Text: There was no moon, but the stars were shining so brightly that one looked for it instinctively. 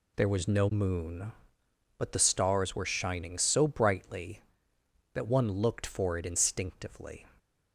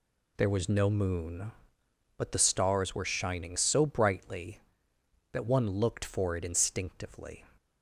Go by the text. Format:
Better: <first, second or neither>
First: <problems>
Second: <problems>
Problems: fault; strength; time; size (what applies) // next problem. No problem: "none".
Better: neither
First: none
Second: none